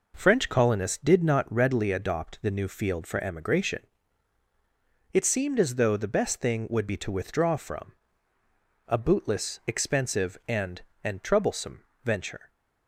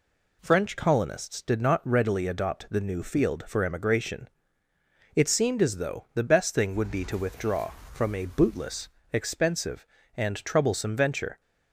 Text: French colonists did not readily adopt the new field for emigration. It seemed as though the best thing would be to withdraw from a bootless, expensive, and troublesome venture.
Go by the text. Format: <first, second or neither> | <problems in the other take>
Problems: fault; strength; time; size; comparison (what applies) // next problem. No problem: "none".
second | pauses between "from" and "a"; noticeable; at 7.9 s; 0.94 s long // says "and" twice; at 11.0 s // pauses between "troublesome" and "venture"; slight; at 11.8 s; 0.20 s long